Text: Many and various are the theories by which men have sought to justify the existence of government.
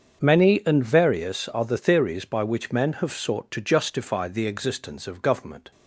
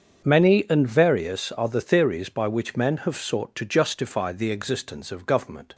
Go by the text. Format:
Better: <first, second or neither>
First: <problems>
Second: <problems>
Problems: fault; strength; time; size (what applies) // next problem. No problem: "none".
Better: neither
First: starts louder than the rest; until 1.2 s; 7 dB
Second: starts louder than the rest; until 1.3 s; 7 dB